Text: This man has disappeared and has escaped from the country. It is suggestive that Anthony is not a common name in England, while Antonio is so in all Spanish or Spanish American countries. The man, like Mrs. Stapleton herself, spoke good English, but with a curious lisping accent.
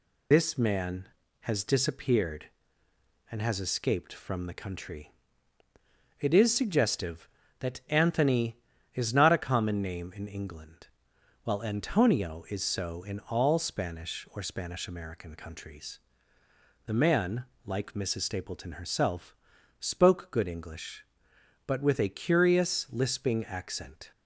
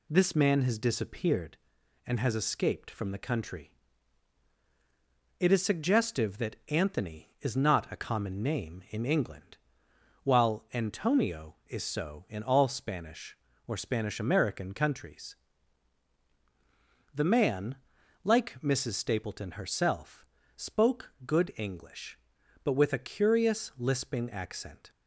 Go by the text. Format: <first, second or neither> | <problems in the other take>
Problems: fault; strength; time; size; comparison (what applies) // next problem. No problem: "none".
second | loses the start of "This"; at 0.3 s; 100 ms